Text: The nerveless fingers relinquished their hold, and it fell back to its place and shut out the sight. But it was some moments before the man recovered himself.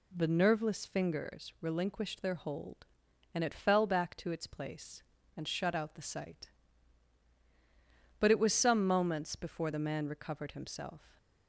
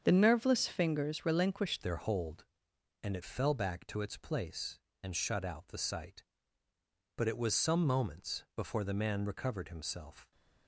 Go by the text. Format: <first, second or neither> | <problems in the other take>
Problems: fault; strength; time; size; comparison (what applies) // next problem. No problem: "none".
first | starts louder than the rest; strong; until 1.0 s; 7 dB // changes voice at "their"; from 1.8 s on; 8.5 s long